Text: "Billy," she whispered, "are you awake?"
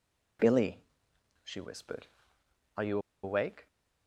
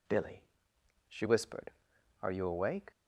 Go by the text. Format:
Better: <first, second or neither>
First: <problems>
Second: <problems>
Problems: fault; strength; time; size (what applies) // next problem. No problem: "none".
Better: second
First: pauses between "you" and "awake"; slight; at 2.9 s; 0.25 s long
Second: none